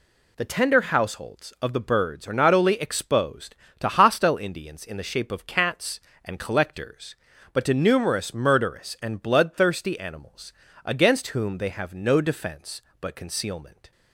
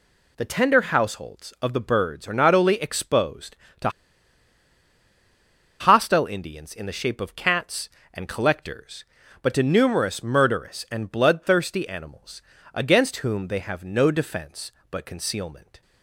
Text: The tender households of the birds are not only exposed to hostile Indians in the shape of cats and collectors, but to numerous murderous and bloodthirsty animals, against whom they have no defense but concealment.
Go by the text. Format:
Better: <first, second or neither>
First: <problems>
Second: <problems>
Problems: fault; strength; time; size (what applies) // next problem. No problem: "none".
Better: first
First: none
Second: pauses between "to" and "hostile"; strong; at 3.8 s; 1.9 s long